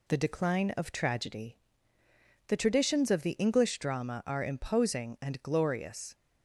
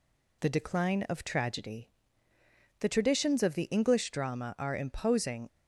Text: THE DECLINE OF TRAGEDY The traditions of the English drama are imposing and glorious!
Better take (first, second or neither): first